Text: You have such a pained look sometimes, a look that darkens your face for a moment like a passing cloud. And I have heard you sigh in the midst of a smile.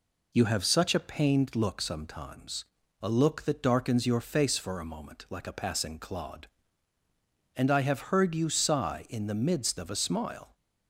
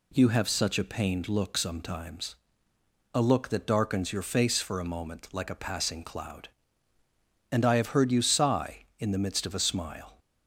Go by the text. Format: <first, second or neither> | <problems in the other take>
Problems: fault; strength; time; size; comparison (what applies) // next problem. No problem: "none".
second | says "clod" for "cloud"; at 5.9 s